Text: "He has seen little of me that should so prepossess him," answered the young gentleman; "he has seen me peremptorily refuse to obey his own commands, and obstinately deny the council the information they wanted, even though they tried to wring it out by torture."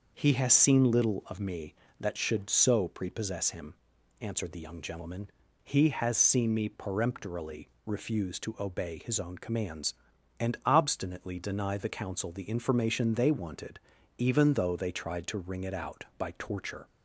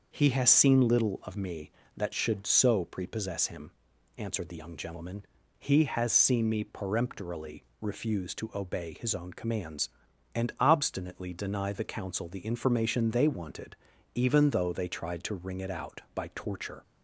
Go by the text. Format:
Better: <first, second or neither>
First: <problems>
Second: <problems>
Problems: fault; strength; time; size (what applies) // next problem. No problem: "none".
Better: neither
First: starts louder than the rest; until 1.1 s; 6.5 dB // pauses between "peremptorily" and "refuse"; slight; at 7.6 s; 0.18 s long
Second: starts louder than the rest; until 1.1 s; 6.5 dB // pauses between "peremptorily" and "refuse"; slight; at 7.6 s; 0.18 s long